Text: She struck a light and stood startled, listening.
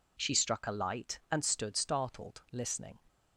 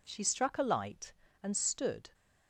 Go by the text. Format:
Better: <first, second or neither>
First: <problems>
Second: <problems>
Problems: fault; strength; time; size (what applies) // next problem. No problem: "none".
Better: first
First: none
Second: stops before "startled listening"; at 2.1 s